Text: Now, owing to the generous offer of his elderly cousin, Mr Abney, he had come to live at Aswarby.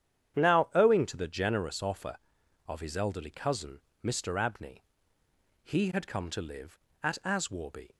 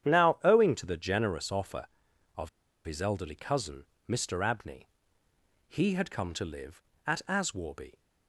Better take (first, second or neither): first